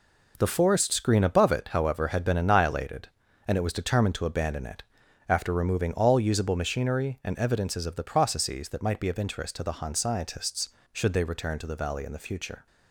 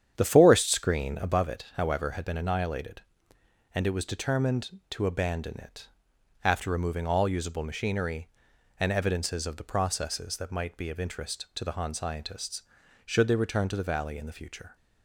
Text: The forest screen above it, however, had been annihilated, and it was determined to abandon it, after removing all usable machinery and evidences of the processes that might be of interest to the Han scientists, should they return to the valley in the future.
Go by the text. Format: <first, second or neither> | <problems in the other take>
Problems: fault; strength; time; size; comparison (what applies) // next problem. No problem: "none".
first | starts louder than the rest; strong; until 1.3 s; 9 dB